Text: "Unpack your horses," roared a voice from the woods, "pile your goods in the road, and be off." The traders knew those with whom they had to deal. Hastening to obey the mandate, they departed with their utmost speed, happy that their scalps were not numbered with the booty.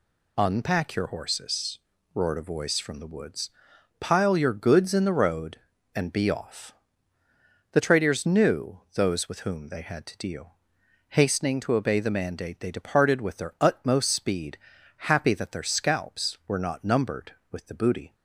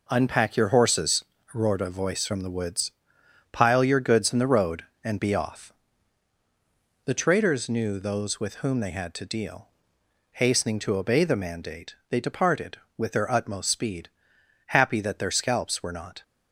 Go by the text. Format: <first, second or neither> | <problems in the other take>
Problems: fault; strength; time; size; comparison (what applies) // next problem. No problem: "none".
first | stops before "numbered with the booty"; at 16.2 s